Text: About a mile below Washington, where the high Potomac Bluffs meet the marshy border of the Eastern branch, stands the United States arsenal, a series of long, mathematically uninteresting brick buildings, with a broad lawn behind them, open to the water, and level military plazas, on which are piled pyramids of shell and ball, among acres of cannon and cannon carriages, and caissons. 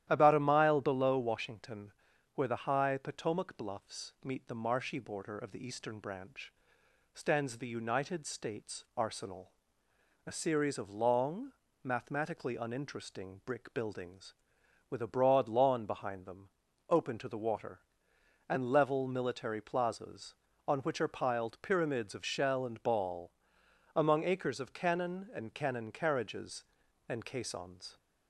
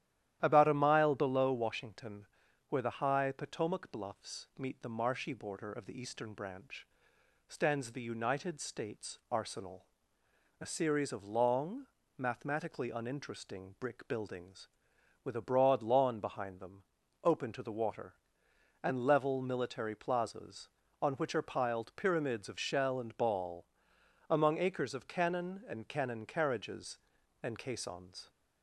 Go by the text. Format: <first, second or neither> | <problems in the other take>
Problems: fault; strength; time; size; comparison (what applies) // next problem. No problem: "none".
neither | starts louder than the rest; strong; the same in both